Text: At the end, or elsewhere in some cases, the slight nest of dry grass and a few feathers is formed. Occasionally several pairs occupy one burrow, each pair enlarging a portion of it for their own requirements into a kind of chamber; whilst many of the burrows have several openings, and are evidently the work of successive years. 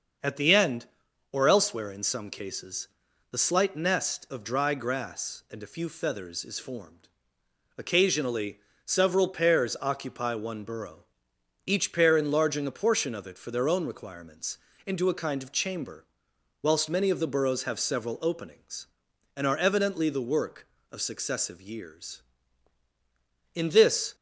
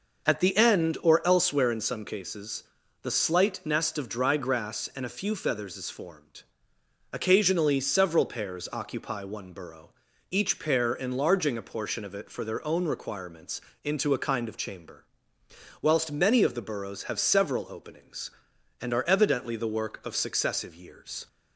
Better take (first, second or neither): second